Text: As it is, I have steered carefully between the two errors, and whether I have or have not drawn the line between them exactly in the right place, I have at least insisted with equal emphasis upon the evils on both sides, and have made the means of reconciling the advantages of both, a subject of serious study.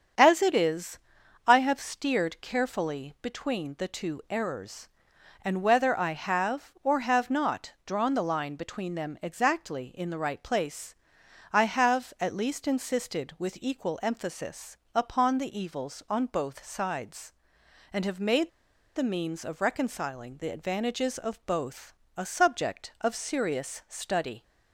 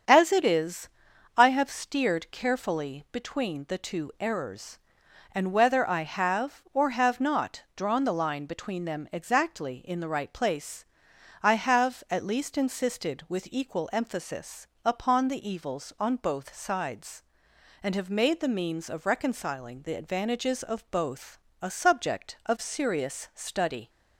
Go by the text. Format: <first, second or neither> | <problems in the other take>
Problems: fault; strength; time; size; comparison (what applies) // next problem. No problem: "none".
second | starts louder than the rest; strong; until 1.6 s; 7.5 dB; strong in the second // pauses between "emphasis" and "upon"; slight; at 14.7 s; 0.16 s long; slight in the second // pauses between "made" and "the"; noticeable; at 18.5 s; 0.46 s long